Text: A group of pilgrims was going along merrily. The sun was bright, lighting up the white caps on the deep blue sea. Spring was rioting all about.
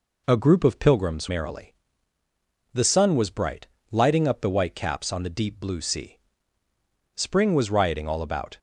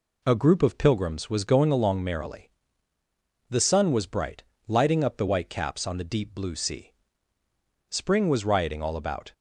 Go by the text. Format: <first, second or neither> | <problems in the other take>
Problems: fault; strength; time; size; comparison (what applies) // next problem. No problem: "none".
second | skips "was going along"; at 1.2 s